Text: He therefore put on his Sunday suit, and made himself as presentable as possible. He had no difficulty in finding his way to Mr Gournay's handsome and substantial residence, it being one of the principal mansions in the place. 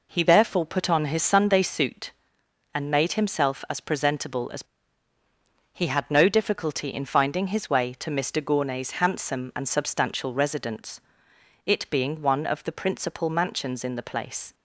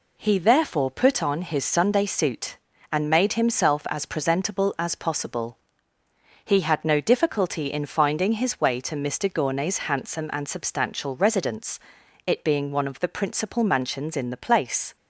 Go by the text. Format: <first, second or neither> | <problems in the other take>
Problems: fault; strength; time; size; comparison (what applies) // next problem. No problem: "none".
second | skips "possible"; at 5.1 s